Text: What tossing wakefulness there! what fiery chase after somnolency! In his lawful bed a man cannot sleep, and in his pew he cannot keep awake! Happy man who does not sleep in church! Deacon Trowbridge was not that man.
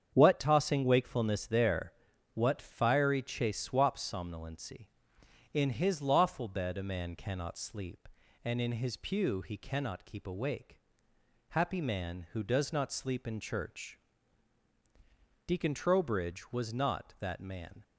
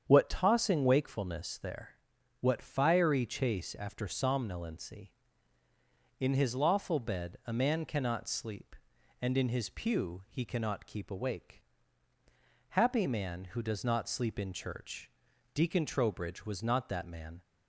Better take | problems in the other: second | starts louder than the rest; strong; until 1.1 s; 8 dB; strong in the second // says "swaps" for "after"; at 3.5 s

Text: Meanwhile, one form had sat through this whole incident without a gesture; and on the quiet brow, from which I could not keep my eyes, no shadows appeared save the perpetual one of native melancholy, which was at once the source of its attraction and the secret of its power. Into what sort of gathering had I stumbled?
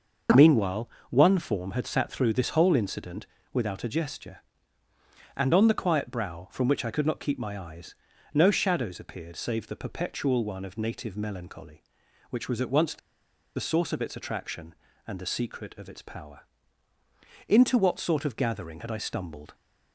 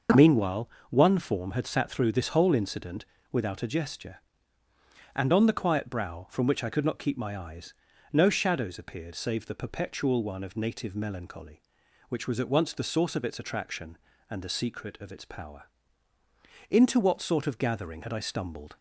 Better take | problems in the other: second | pauses between "incident" and "without"; slight; at 3.2 s; 0.26 s long; slight in the second // pauses between "the" and "source"; noticeable; at 12.9 s; 0.58 s long

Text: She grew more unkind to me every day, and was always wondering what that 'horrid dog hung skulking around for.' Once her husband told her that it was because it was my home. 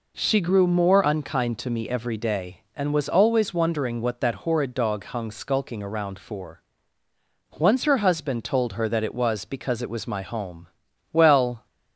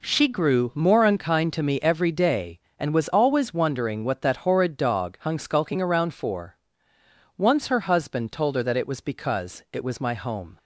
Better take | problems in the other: second | goes on to say "Well"; from 11.1 s on; 0.54 s long

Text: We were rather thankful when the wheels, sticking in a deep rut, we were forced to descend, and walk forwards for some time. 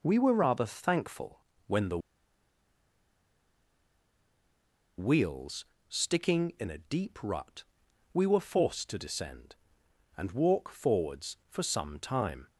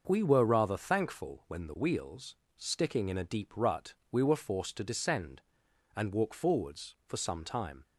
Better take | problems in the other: second | pauses between "thankful" and "when"; slight; at 1.3 s; 0.28 s long // pauses between "the" and "wheels"; strong; at 1.9 s; 2.9 s long

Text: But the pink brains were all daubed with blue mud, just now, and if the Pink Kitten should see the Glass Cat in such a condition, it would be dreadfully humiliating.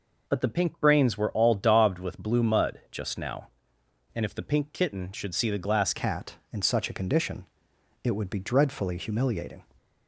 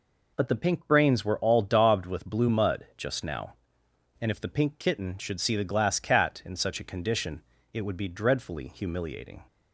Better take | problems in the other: second | changes voice at "Cat"; from 5.9 s on; 3.7 s long

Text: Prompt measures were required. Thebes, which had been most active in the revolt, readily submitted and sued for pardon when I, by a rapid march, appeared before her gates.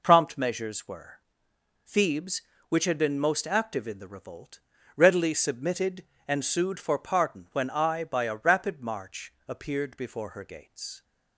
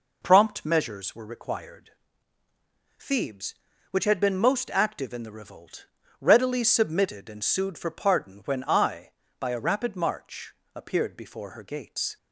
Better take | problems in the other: second | skips "required"; at 1.5 s

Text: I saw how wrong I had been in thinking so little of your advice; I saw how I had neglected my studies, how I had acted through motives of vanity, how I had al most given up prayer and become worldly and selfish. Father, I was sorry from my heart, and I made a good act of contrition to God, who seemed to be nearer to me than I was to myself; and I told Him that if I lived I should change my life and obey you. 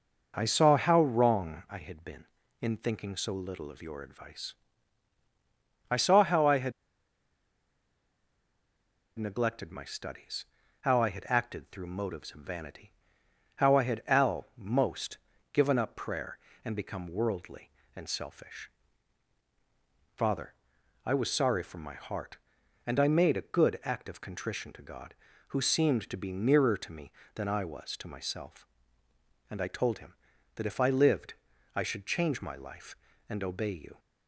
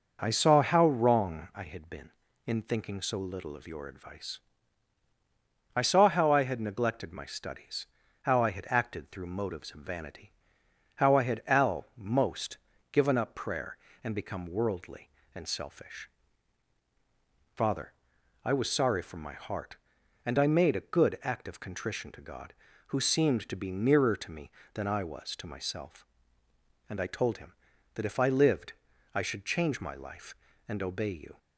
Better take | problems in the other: second | pauses between "had" and "neglected"; strong; at 6.7 s; 2.4 s long // pauses between "most" and "given"; slight; at 15.1 s; 0.34 s long; slight in the second // pauses between "lived" and "I"; at 31.3 s; 0.42 s long; also in the second

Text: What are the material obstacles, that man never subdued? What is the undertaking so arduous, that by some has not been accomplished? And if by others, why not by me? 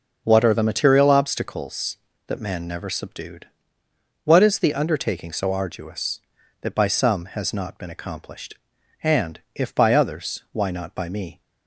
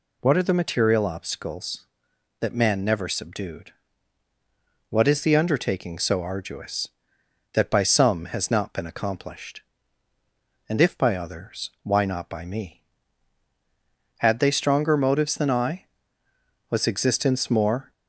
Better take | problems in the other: first | goes on to say "Had they stronger motives than I Was existence more"; strong; from 14.1 s on; 3.7 s long

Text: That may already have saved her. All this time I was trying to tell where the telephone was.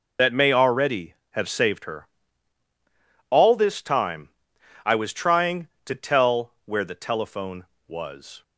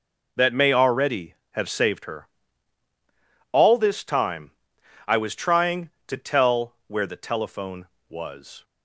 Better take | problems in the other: second | loses the start of "That"; at 0.1 s; 55 ms // pauses between "time" and "I"; noticeable; at 4.3 s; 0.54 s long; noticeable in the second

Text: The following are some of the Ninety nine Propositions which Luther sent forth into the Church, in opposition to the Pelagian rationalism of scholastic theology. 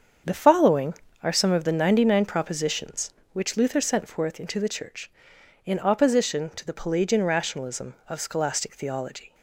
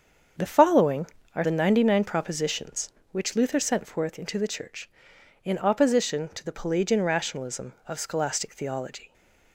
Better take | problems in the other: first | starts louder than the rest; until 1.6 s; 7 dB; strong in the first // skips "some of"; at 1.4 s

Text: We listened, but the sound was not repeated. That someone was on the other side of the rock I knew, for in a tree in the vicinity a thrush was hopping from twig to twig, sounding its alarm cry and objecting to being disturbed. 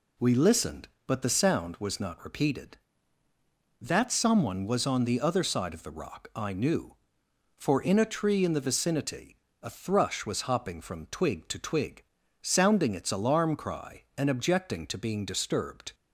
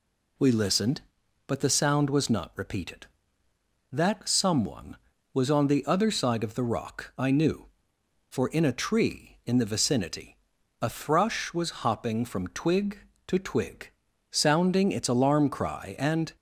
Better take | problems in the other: first | pauses between "vicinity" and "a"; at 10.3 s; 0.44 s long; slight in the first // stops before "objecting to being disturbed"; at 16.3 s

